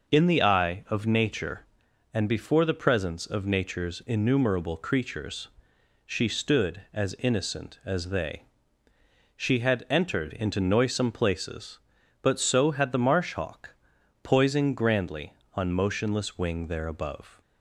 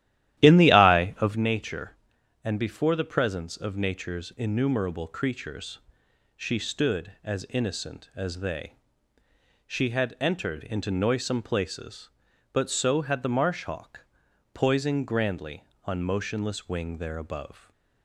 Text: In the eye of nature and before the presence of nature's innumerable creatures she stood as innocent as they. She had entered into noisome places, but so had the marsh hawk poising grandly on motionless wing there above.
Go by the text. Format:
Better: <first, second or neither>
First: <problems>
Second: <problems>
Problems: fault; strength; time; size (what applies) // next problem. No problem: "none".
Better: first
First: pauses between "creatures" and "she"; noticeable; at 5.4 s; 0.56 s long // pauses between "hawk" and "poising"; noticeable; at 13.7 s; 0.48 s long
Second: starts louder than the rest; strong; until 1.4 s; 13.5 dB // pauses between "creatures" and "she"; noticeable; at 5.7 s; 0.56 s long // pauses between "hawk" and "poising"; noticeable; at 14.0 s; 0.48 s long // stays silent after the last word; slight; from 17.5 s on; 0.5 s long